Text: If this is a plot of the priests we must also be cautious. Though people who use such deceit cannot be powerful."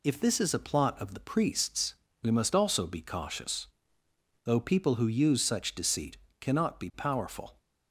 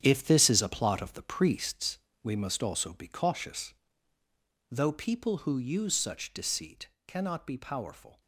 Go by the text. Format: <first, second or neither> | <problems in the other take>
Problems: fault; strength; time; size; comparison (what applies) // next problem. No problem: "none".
first | gets quieter; strong; throughout; 10.5 dB // pauses between "priests" and "we"; slight; at 1.9 s; 0.24 s long; slight in the first // pauses between "deceit" and "cannot"; slight; at 6.8 s; 0.18 s long; slight in the first